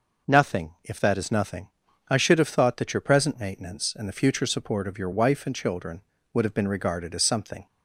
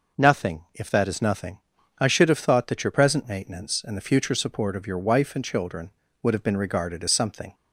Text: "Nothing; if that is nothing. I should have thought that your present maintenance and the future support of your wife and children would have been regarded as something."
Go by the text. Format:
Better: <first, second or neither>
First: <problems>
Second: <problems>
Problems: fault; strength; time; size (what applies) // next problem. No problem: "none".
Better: neither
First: none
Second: none